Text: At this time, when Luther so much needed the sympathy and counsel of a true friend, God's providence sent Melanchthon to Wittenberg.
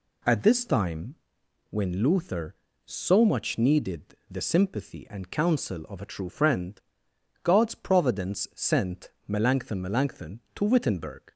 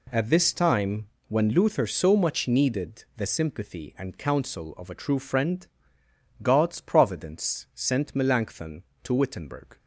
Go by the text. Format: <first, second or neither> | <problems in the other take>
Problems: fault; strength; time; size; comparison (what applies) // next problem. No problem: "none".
second | pauses between "needed" and "the"; slight; at 4.1 s; 0.16 s long // pauses between "sent" and "Melanchthon"; slight; at 9.0 s; 0.18 s long // says "Melanchthon" twice; at 9.8 s